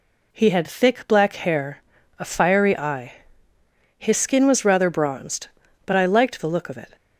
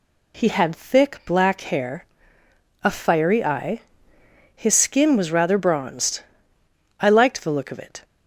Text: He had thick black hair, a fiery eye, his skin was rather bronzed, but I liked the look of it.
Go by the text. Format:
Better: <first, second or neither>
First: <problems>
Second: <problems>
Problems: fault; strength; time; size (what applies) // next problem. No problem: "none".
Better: first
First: none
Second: skips "but"; at 6.6 s